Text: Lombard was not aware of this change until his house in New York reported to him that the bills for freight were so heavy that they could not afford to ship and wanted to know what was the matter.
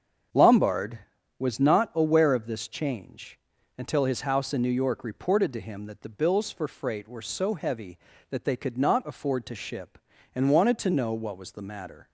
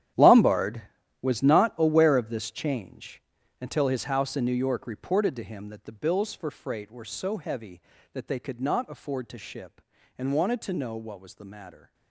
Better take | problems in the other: first | gets quieter; strong; throughout; 16 dB // starts louder than the rest; strong; until 1.5 s; 11.5 dB; strong in the first // pauses between "change" and "until"; at 3.1 s; 0.40 s long; also in the first

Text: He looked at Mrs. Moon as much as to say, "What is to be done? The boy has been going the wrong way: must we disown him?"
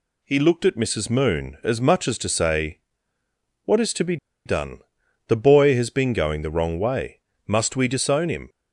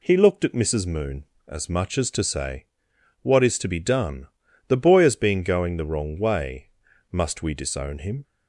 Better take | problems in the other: second | pauses between "be" and "done"; slight; at 4.1 s; 0.29 s long

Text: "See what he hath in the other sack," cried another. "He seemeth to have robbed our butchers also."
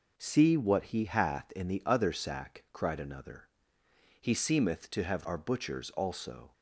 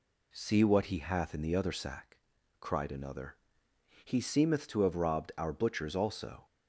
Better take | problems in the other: second | skips "robbed"; at 5.2 s

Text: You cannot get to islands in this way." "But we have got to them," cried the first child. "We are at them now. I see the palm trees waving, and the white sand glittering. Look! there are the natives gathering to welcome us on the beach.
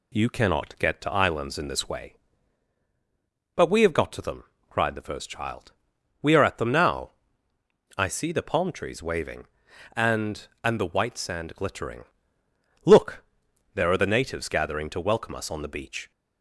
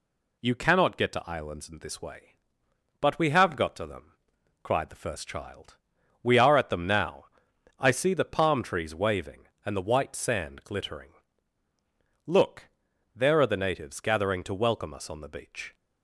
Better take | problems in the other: second | says "and" twice; at 10.6 s

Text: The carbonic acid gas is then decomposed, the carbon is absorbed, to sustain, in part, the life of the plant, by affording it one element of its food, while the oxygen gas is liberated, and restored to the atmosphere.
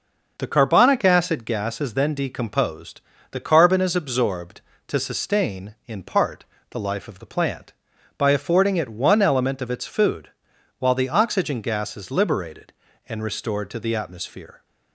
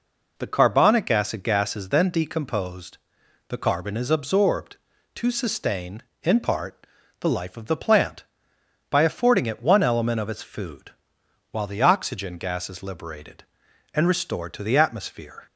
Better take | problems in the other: neither | none

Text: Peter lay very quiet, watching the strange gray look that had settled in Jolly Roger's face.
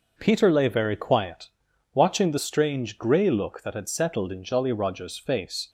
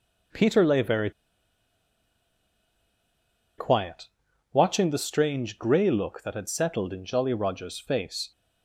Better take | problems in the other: first | pauses between "very" and "quiet"; strong; at 1.1 s; 2.4 s long

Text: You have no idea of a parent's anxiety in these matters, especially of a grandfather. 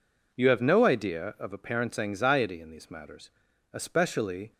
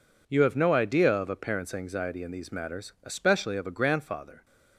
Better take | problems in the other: second | stops before "of a grandfather"; at 4.5 s

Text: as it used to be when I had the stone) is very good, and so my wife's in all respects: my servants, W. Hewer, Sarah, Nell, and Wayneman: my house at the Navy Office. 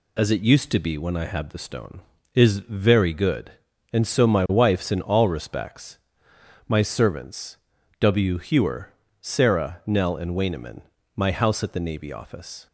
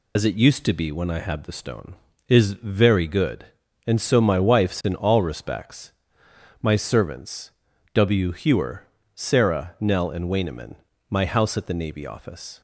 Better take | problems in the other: first | loses the start of "as"; at 0.1 s; 45 ms

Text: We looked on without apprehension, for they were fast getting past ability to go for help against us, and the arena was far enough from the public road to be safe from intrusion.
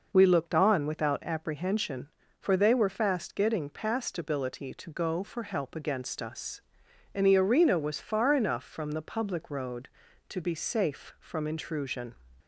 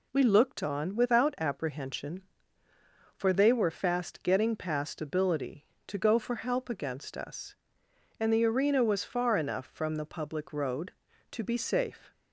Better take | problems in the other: first | stops before "from intrusion"; at 12.1 s

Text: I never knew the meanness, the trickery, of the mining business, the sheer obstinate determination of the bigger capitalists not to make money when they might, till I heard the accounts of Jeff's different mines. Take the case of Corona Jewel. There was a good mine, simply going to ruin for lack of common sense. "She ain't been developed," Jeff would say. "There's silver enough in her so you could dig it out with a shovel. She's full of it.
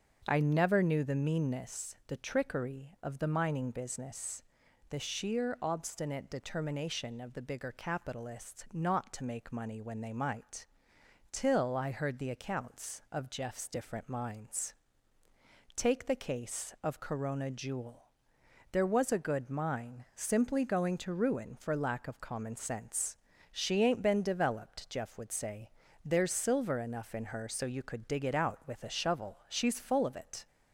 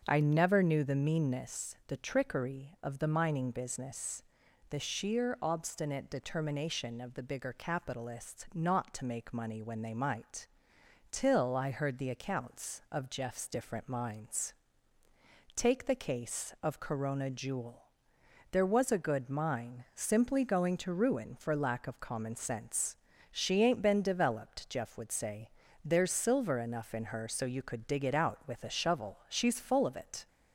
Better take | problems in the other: neither | starts louder than the rest; the same in both

